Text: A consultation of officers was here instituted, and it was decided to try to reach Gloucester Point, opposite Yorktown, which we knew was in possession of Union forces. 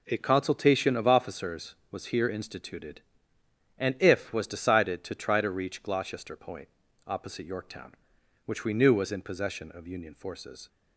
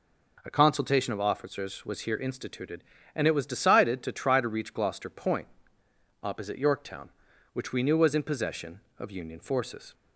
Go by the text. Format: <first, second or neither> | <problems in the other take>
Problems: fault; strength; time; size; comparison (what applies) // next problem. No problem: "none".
second | says "if" for "it"; at 3.9 s